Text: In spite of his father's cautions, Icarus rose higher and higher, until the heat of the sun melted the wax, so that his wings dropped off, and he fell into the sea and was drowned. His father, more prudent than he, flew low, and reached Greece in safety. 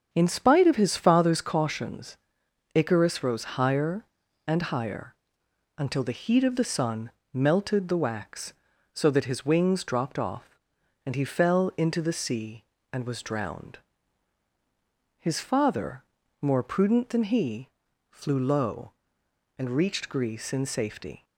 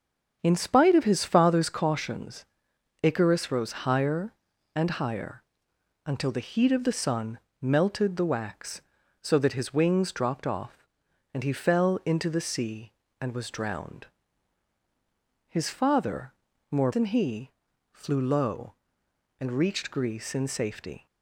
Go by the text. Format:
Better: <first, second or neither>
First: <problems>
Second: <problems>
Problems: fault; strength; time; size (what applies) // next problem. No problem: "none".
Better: first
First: starts louder than the rest; strong; until 1.1 s; 7.5 dB // pauses between "sun" and "melted"; slight; at 7.1 s; 0.22 s long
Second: starts louder than the rest; strong; until 1.4 s; 7.5 dB // pauses between "sun" and "melted"; slight; at 7.3 s; 0.22 s long // skips "prudent"; at 16.9 s